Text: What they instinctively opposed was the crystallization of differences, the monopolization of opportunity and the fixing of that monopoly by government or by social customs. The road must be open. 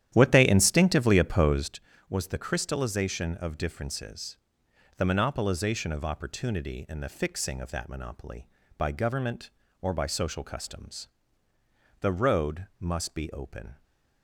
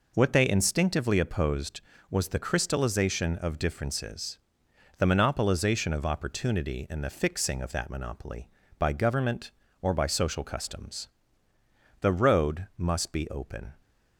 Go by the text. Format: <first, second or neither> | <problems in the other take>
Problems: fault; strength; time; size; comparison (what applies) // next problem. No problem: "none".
second | starts louder than the rest; strong; until 1.8 s; 11 dB